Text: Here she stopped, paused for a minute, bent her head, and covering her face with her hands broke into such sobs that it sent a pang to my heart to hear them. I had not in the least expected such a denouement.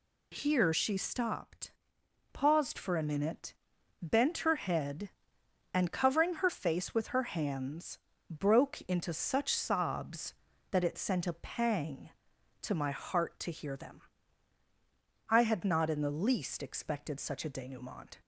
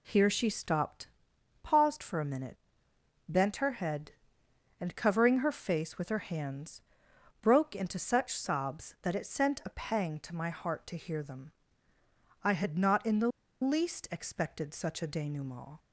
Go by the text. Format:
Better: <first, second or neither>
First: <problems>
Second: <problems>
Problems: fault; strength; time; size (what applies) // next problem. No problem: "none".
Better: first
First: pauses between "hands" and "broke"; slight; at 7.9 s; 0.32 s long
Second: pauses between "hands" and "broke"; noticeable; at 6.7 s; 0.62 s long // pauses between "the" and "least"; slight; at 13.2 s; 0.33 s long